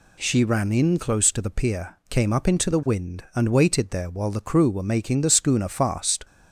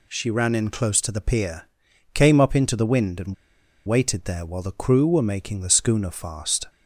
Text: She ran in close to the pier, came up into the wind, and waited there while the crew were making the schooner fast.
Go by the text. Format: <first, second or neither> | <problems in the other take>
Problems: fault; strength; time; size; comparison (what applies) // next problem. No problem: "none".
first | pauses between "and" and "waited"; noticeable; at 3.3 s; 0.52 s long